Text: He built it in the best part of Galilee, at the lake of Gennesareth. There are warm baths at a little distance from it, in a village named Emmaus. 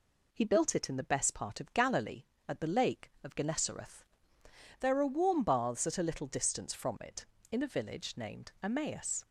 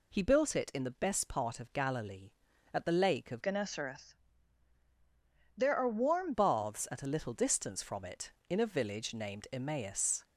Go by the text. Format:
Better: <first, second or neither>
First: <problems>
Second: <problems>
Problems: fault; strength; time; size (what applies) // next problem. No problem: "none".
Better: first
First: none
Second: changes voice from "Gennesareth" to "warm"; from 3.4 to 6.3 s; 2.9 s long